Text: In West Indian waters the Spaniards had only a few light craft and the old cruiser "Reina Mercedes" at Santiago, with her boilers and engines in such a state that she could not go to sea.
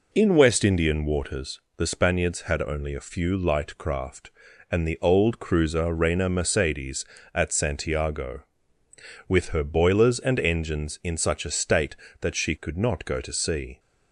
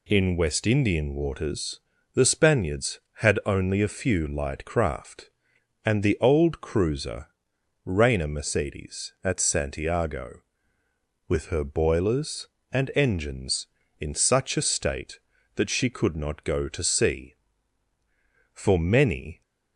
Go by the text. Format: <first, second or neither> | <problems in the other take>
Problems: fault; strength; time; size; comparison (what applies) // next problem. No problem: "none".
first | pauses between "waters" and "the"; slight; at 1.8 s; 0.32 s long; slight in the first // pauses between "cruiser" and "Reina"; noticeable; at 7.2 s; 0.56 s long // goes on to say "For many"; noticeable; from 18.5 s on; 0.88 s long